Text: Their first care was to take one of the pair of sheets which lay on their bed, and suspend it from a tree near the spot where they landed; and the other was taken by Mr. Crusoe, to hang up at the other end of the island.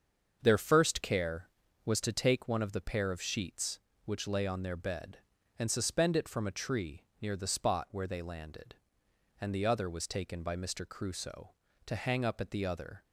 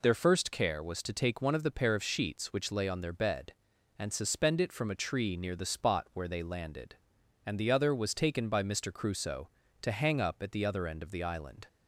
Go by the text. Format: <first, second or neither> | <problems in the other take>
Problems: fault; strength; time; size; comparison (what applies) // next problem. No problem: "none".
second | starts louder than the rest; until 1.4 s; 7 dB // stops before "end of the island"; at 13.0 s